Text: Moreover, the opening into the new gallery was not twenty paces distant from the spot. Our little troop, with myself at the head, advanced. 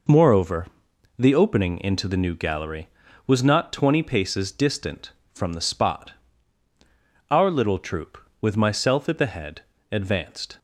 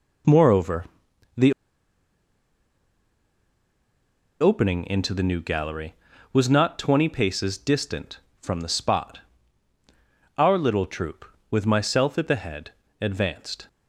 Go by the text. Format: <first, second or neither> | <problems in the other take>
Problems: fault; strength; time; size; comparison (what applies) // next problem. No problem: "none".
first | pauses between "the" and "opening"; strong; at 1.5 s; 2.8 s long